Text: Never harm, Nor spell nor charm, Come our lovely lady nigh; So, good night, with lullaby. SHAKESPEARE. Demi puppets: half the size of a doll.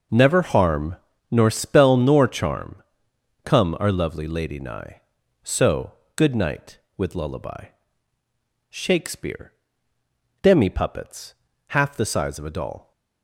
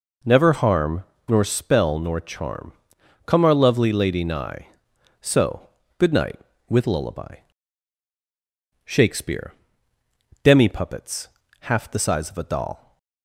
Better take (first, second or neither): neither